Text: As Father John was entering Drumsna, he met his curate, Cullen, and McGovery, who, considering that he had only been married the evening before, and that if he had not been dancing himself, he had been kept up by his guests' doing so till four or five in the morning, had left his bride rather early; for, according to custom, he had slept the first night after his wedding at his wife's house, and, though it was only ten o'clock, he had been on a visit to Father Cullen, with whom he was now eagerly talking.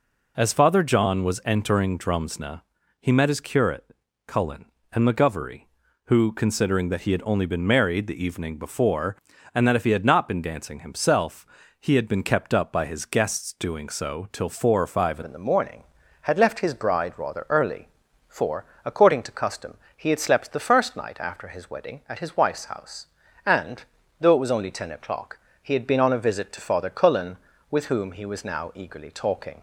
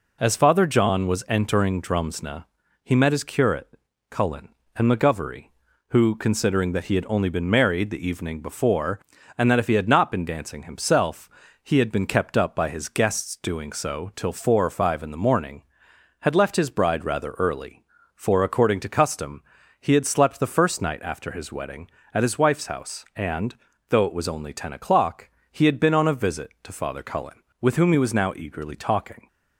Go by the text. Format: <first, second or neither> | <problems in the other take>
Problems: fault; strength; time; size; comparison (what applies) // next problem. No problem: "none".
second | changes voice at "in"; from 15.2 s on; 14.4 s long